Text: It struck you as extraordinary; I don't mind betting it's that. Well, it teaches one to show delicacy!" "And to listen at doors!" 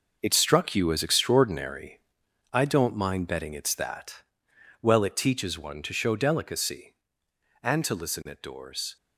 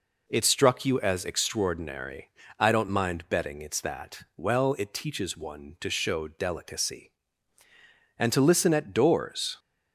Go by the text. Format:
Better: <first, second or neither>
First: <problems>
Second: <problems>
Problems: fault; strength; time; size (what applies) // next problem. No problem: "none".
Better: second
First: gets quieter; strong; throughout; 10 dB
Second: none